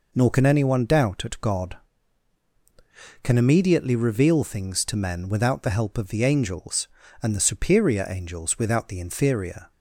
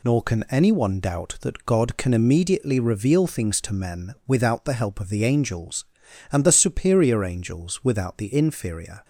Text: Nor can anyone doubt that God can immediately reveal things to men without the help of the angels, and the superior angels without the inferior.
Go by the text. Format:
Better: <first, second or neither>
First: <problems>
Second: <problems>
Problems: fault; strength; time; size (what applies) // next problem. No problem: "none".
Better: second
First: says "at" for "that"; at 1.2 s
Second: none